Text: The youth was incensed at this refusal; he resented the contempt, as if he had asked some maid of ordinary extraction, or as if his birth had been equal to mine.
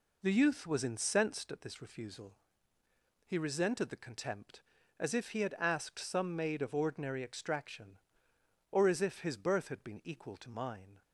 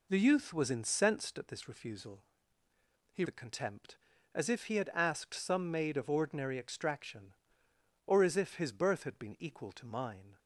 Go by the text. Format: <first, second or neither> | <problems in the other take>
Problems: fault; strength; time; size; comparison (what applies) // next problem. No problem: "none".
first | skips "resented"; at 3.2 s